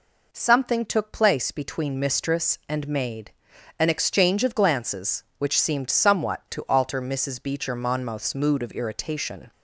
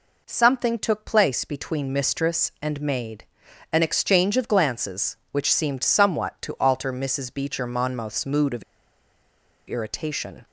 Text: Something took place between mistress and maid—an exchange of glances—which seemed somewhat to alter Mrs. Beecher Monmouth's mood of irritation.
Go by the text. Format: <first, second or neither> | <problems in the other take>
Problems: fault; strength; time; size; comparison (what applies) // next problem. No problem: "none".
first | pauses between "of" and "irritation"; at 8.6 s; 1.0 s long